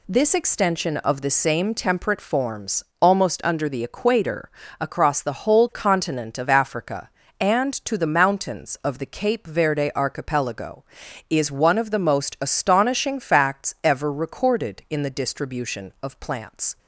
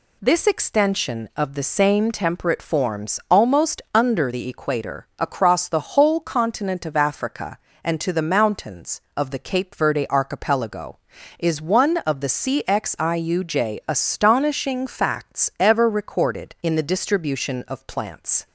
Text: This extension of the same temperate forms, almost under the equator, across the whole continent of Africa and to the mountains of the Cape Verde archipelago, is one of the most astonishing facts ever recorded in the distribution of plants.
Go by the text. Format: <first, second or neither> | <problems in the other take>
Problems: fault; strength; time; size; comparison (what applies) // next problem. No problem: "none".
first | says "cxiuj" for "most"; at 12.2 s